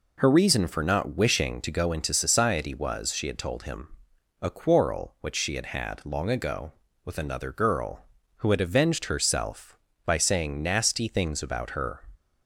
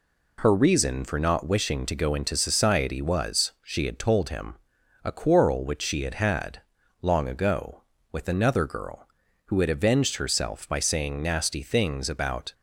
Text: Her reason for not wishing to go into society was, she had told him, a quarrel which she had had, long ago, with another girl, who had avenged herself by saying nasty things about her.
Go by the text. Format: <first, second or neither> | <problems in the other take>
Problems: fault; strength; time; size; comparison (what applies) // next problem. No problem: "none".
first | stops before "her"; at 12.5 s